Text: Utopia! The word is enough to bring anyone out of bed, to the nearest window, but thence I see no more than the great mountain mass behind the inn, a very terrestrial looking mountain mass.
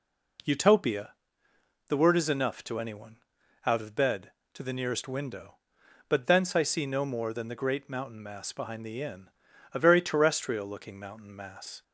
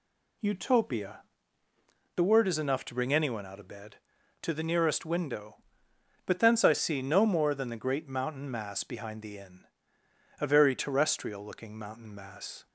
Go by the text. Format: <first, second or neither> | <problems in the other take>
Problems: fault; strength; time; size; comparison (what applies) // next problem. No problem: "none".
second | skips "bring"; at 2.7 s // pauses between "anyone" and "out"; noticeable; at 3.1 s; 0.50 s long